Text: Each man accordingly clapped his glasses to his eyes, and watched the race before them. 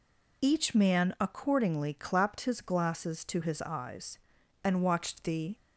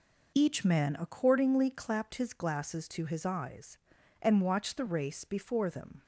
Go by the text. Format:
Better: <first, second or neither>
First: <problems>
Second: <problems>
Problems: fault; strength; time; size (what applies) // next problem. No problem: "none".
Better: second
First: stops before "race before them"; at 5.5 s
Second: none